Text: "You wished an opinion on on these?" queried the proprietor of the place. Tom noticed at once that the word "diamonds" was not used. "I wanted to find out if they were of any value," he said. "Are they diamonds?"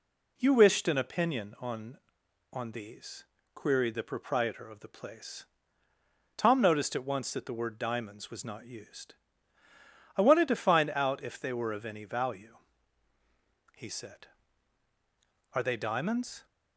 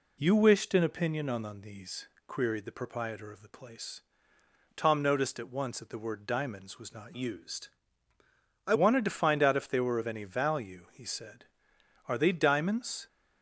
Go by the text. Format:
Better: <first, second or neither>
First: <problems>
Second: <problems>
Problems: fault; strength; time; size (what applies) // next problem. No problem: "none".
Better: first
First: none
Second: changes voice from "used" to "I"; from 7.1 to 8.7 s; 1.6 s long